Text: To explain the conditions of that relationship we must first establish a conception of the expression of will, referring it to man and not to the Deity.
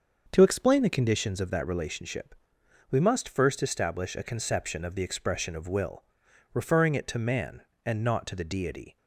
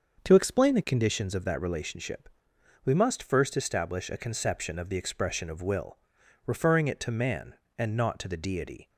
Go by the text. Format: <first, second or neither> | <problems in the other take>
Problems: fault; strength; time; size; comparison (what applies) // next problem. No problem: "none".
neither | starts louder than the rest; the same in both // pauses between "relationship" and "we"; noticeable; the same in both